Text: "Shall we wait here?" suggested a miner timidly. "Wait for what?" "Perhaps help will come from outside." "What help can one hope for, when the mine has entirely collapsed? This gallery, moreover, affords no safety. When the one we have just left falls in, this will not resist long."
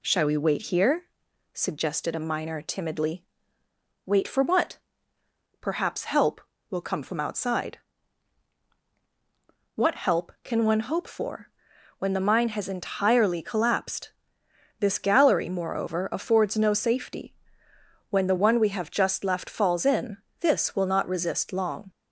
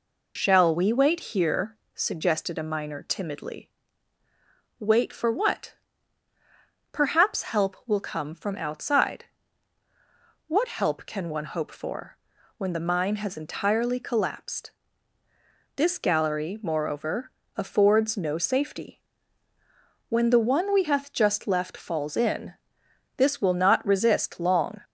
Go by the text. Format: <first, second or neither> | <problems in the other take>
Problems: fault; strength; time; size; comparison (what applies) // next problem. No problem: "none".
first | says "hath" for "have"; at 20.8 s